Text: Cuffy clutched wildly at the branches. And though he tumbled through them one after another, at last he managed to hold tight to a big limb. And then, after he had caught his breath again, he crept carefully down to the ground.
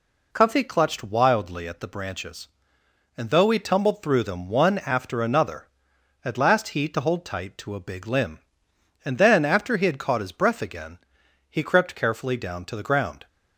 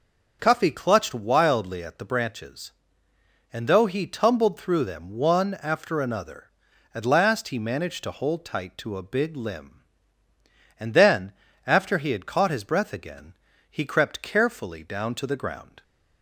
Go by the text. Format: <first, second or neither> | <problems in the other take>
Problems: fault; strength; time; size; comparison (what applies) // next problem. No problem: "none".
second | skips "managed"; at 6.8 s